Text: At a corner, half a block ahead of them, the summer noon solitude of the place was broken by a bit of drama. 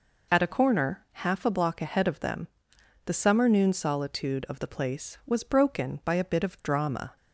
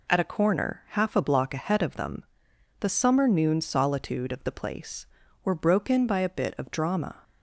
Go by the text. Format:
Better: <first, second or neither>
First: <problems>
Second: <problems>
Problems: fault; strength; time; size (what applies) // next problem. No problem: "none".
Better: first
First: none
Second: says "were" for "was"; at 5.4 s